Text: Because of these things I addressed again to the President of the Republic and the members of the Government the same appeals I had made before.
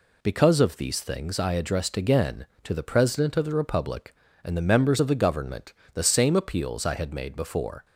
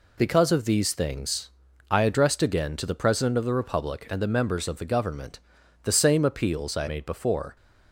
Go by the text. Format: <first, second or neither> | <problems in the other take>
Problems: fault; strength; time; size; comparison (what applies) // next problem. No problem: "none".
first | pauses between "things" and "I"; at 1.4 s; 0.40 s long // pauses between "Government" and "the"; noticeable; at 5.3 s; 0.46 s long; slight in the first // skips "had"; at 6.8 s